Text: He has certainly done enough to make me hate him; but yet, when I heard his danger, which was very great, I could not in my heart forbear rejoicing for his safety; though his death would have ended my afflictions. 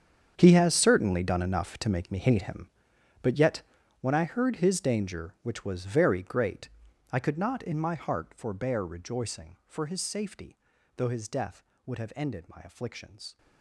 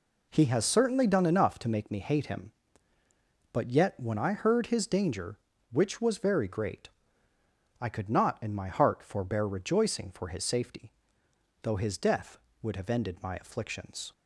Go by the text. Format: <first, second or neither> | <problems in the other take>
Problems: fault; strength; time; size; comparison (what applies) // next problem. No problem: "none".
second | gets quieter; strong; throughout; 16.5 dB